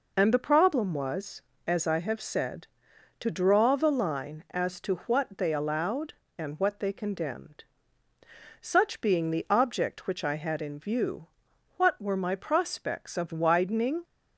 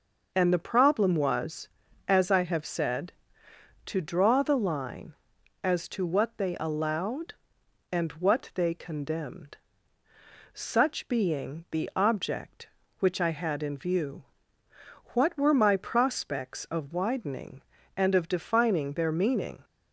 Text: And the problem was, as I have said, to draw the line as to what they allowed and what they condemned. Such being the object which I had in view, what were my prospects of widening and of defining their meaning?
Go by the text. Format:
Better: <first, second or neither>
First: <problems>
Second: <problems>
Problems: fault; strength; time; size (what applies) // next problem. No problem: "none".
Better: second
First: stops before "and of defining their meaning"; at 14.0 s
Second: none